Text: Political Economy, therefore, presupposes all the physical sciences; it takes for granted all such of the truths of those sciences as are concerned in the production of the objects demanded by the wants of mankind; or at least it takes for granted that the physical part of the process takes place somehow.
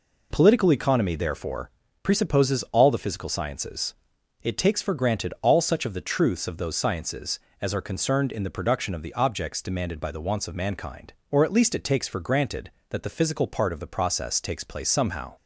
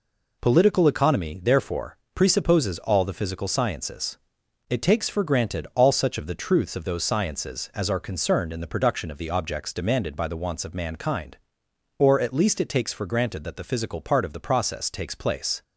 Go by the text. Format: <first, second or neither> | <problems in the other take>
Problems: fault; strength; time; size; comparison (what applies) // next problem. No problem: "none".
first | stops before "somehow"; at 15.6 s